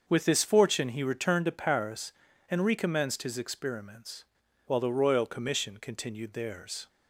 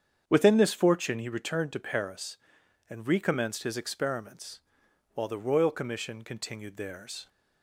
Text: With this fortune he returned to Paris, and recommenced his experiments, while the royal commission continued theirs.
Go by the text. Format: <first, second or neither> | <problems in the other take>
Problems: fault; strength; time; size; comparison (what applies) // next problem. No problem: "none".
first | starts louder than the rest; strong; until 1.2 s; 8 dB; also in the first // says "Within" for "With"; at 0.2 s